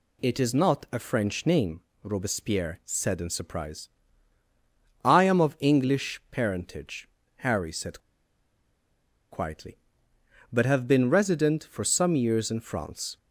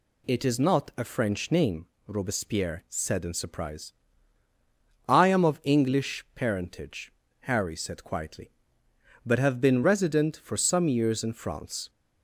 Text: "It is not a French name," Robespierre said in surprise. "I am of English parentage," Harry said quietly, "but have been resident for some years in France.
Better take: second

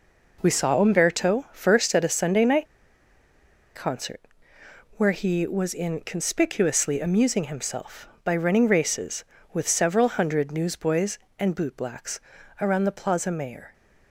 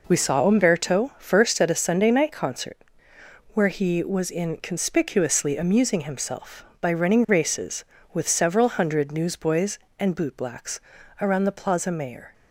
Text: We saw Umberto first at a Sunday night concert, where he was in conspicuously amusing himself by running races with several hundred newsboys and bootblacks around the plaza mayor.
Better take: second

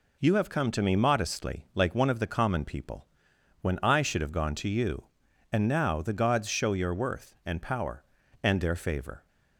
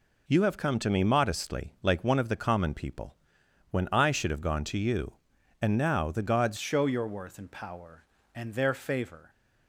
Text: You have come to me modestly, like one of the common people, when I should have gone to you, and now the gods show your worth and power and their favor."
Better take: first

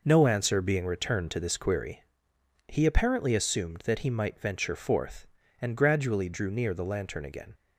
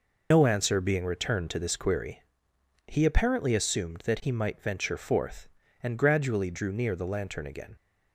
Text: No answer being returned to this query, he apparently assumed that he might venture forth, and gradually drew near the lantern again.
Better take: first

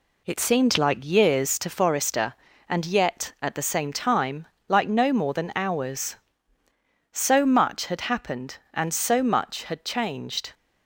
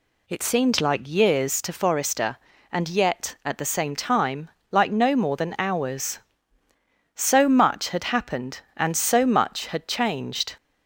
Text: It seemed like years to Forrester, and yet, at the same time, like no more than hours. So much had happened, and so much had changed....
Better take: second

